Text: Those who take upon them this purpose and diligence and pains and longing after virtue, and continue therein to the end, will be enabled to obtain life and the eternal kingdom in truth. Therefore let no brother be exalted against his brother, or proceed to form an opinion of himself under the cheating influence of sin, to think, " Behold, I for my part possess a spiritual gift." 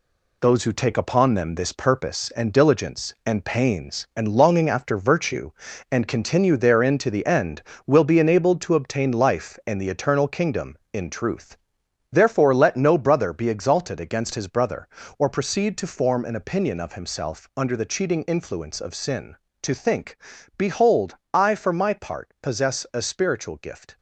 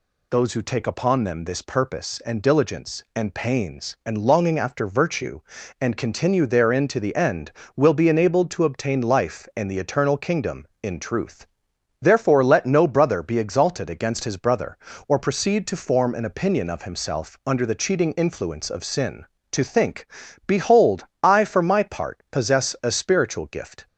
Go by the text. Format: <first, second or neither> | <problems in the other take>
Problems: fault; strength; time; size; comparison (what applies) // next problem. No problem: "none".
second | gets quieter; strong; throughout; 8 dB